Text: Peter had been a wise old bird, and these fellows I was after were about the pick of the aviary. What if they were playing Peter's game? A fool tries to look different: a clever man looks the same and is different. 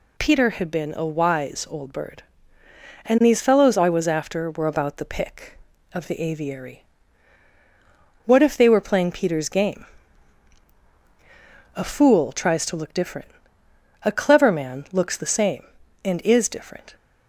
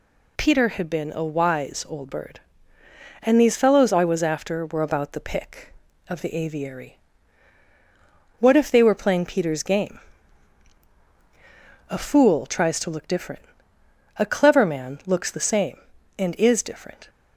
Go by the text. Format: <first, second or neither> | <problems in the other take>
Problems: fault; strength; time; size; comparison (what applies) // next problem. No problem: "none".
neither | none